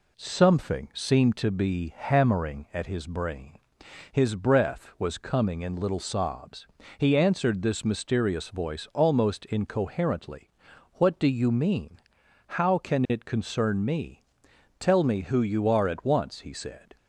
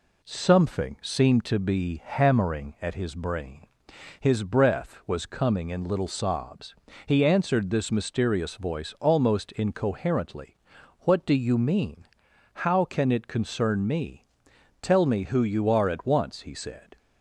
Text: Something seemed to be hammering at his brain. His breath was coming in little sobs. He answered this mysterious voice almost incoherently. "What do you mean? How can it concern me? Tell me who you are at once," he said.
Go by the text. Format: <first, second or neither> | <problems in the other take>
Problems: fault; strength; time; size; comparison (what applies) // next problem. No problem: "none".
neither | none